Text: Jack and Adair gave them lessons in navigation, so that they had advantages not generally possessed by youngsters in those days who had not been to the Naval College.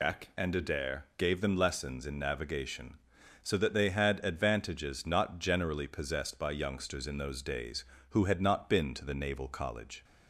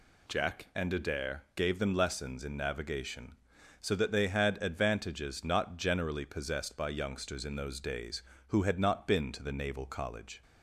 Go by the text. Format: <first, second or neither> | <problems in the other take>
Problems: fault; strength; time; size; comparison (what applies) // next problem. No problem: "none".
second | loses the start of "Jack"; at 0.0 s; 115 ms